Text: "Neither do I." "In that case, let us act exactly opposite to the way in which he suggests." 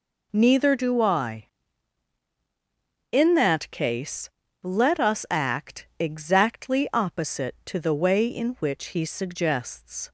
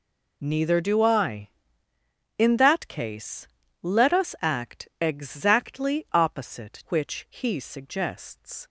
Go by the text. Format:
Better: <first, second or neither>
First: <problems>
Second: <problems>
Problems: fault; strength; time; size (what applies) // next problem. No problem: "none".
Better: first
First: none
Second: skips "to the way in"; at 6.8 s